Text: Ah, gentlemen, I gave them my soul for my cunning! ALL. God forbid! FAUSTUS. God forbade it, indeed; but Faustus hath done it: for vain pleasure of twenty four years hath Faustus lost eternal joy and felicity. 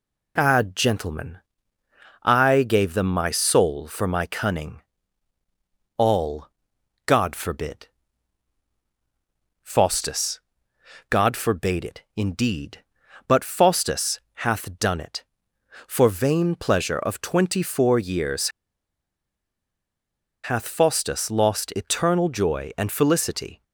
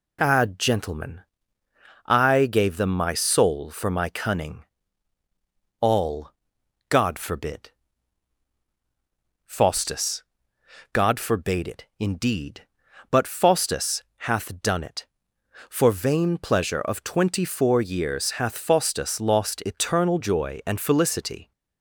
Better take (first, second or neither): second